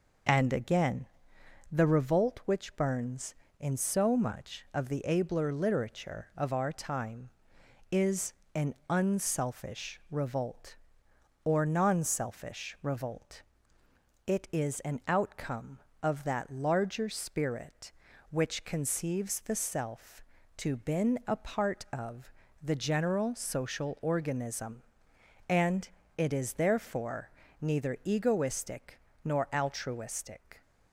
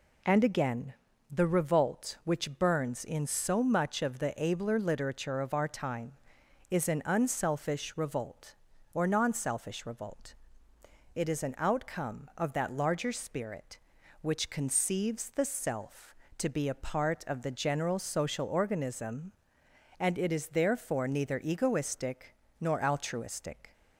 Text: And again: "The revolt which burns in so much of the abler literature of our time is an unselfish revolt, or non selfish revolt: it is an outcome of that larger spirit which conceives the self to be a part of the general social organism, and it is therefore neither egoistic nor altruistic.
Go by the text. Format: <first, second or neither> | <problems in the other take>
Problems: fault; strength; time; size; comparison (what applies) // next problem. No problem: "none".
second | pauses between "is" and "an"; slight; at 8.3 s; 0.20 s long // says "been" for "be"; at 20.7 s // pauses between "of" and "the"; slight; at 22.3 s; 0.28 s long // pauses between "and" and "it"; slight; at 25.8 s; 0.30 s long // pauses between "therefore" and "neither"; slight; at 27.2 s; 0.32 s long // pauses between "egoistic" and "nor"; slight; at 28.9 s; 0.24 s long; slight in the second